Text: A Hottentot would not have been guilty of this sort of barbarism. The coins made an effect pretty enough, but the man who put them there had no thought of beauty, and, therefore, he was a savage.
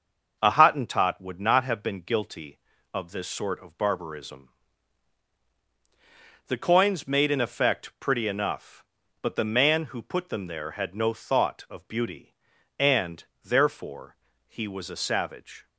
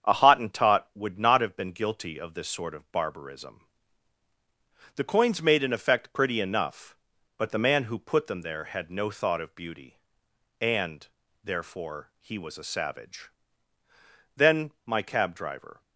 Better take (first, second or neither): first